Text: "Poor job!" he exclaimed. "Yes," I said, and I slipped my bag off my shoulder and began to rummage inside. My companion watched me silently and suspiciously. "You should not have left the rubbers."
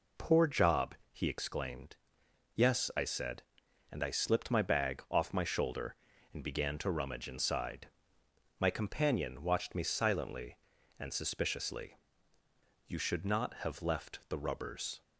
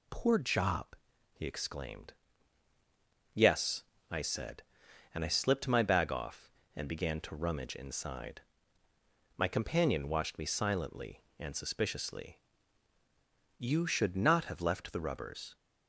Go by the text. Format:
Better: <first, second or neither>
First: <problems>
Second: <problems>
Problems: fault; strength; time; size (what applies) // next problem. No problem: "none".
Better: first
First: none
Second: skips "my shoulder"; at 6.6 s